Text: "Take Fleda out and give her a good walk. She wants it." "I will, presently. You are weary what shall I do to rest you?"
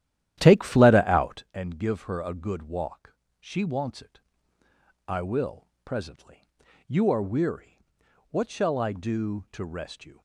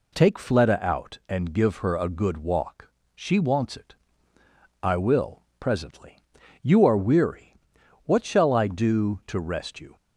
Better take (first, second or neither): second